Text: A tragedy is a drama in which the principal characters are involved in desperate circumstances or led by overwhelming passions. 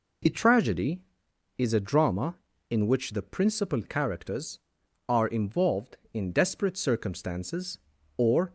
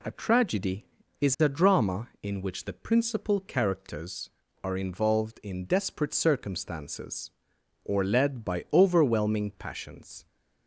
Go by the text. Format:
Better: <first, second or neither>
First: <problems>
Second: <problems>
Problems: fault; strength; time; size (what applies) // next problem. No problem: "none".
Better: second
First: stops before "led by overwhelming passions"; at 8.4 s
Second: none